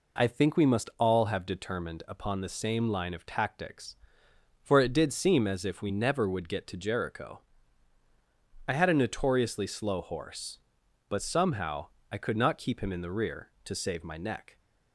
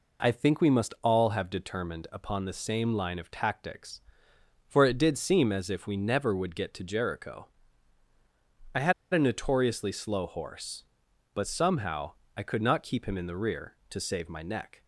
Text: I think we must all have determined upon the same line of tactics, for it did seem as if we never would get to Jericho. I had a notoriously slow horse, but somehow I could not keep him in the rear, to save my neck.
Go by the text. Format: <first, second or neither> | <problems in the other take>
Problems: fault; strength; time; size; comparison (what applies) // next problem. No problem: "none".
first | pauses between "had" and "a"; slight; at 8.9 s; 0.20 s long // pauses between "somehow" and "I"; slight; at 12.1 s; 0.24 s long; slight in the first